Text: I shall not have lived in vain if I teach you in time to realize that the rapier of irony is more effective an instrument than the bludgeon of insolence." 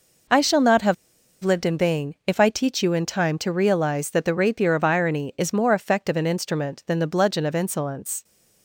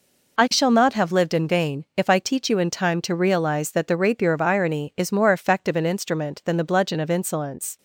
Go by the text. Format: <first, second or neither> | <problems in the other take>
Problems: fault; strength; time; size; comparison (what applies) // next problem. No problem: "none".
second | pauses between "have" and "lived"; noticeable; at 0.9 s; 0.48 s long